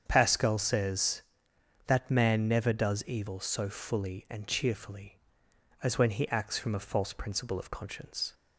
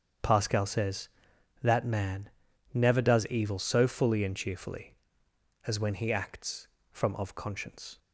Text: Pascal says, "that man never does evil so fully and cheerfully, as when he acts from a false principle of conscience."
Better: first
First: starts louder than the rest; strong; until 1.0 s; 7.5 dB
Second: starts louder than the rest; strong; until 1.7 s; 8 dB // pauses between "man" and "never"; noticeable; at 2.2 s; 0.46 s long // skips "a false principle"; at 7.1 s

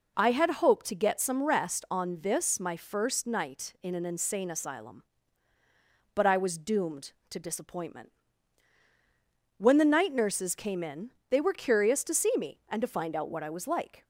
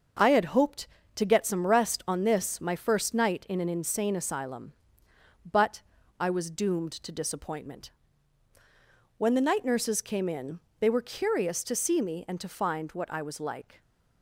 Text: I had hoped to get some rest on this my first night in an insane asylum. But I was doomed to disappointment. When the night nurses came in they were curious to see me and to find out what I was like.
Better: first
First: pauses between "in" and "they"; slight; at 11.1 s; 0.18 s long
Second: starts louder than the rest; until 1.4 s; 6.5 dB // pauses between "But" and "I"; at 5.8 s; 0.38 s long // pauses between "in" and "they"; slight; at 10.5 s; 0.22 s long // skips "out"; at 12.9 s

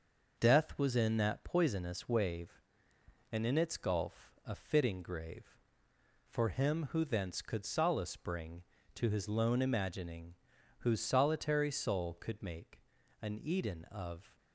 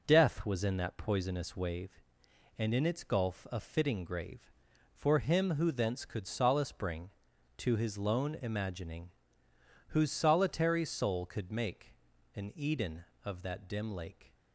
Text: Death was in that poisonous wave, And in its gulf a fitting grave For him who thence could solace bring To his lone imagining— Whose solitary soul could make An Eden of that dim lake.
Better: second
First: starts louder than the rest; noticeable; until 1.4 s; 6 dB // pauses between "make" and "An"; at 12.8 s; 0.40 s long // stops before "that dim lake"; at 14.3 s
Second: pauses between "make" and "An"; at 11.9 s; 0.42 s long

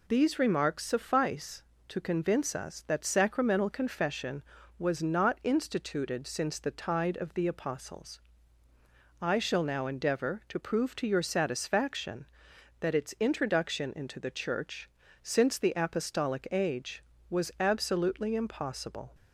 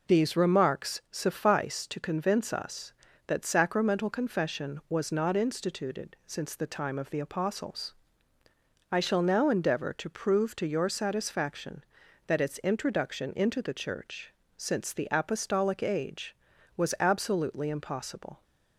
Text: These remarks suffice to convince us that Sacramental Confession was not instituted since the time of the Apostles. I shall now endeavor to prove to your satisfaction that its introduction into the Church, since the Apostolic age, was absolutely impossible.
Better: second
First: says "tide" for "time"; at 6.7 s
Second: none

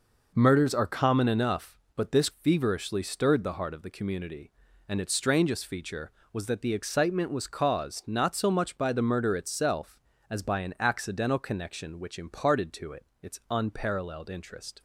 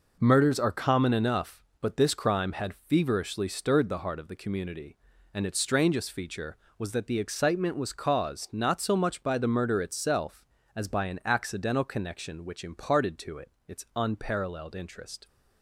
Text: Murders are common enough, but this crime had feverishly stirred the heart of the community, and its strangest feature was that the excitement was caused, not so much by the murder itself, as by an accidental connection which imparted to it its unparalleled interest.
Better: second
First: skips "crime had"; at 2.2 s // pauses between "it" and "its"; slight; at 13.0 s; 0.16 s long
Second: pauses between "it" and "its"; slight; at 13.5 s; 0.16 s long

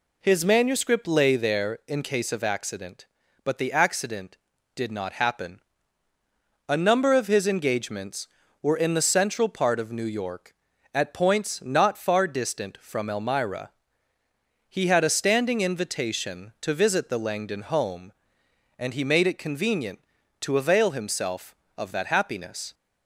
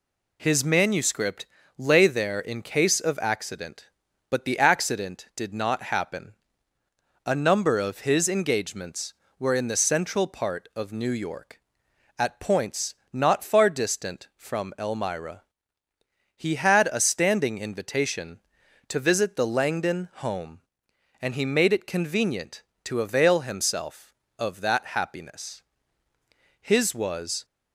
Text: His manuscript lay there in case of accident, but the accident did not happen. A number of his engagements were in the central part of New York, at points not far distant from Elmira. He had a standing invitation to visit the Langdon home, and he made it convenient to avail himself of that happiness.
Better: first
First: none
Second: pauses between "manuscript" and "lay"; slight; at 1.4 s; 0.32 s long // pauses between "points" and "not"; slight; at 12.9 s; 0.18 s long // goes on to say "His was"; noticeable; from 26.5 s on; 0.86 s long

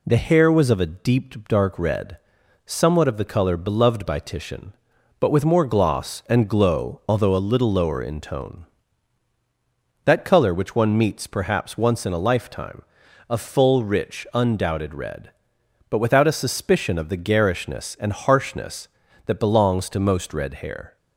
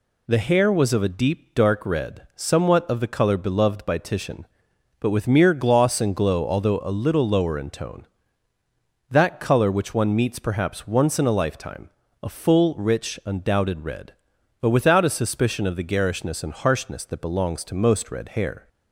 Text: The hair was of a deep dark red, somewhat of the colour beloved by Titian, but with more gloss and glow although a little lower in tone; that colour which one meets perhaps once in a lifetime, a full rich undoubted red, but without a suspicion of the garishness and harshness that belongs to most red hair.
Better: first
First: none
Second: says "mere" for "more"; at 5.2 s

